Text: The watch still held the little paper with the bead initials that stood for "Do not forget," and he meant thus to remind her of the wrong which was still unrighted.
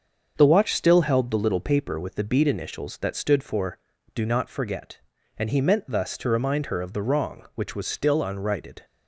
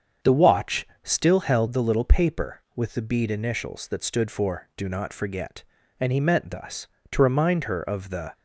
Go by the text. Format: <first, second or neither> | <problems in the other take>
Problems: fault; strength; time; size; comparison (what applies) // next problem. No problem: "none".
first | starts louder than the rest; strong; until 1.4 s; 7.5 dB; also in the first // pauses between "watch" and "still"; slight; at 0.8 s; 0.16 s long // stops before "wrong which was still unrighted"; at 8.3 s